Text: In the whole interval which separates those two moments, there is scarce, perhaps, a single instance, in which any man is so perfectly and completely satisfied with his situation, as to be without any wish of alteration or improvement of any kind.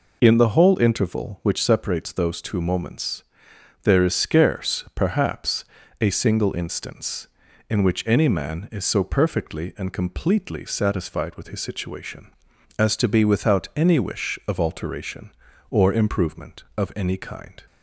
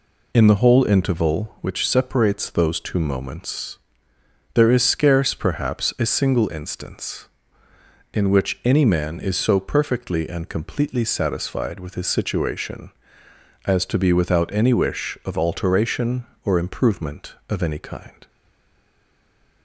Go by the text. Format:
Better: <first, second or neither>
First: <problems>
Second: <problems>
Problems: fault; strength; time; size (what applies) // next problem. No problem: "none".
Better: first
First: none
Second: stays silent after the last word; noticeable; from 18.2 s on; 1.4 s long